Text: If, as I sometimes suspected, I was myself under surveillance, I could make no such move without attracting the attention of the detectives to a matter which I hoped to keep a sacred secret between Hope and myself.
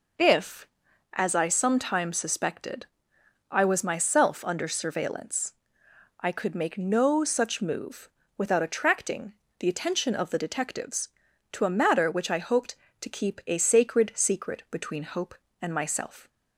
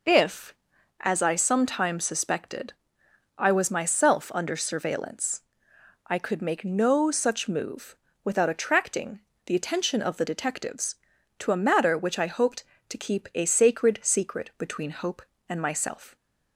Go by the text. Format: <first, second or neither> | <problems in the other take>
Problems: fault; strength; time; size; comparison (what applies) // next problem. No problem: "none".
neither | pauses between "move" and "without"; slight; the same in both // pauses between "attracting" and "the"; slight; the same in both